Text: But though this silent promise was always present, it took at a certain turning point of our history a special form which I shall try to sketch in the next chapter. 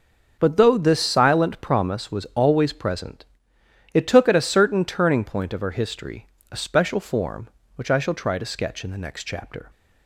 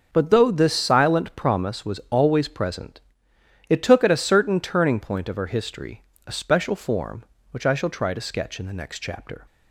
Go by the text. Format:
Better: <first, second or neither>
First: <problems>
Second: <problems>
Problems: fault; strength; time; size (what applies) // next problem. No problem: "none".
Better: neither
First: starts louder than the rest; until 1.3 s; 6.5 dB // pauses between "history" and "a"; slight; at 6.2 s; 0.24 s long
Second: starts louder than the rest; until 1.1 s; 6.5 dB // pauses between "history" and "a"; slight; at 6.0 s; 0.24 s long